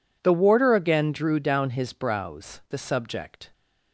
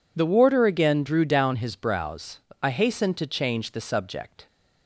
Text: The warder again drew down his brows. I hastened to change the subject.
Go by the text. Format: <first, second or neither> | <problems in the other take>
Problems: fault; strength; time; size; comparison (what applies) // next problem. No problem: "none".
second | skips "I hastened to change"; at 2.6 s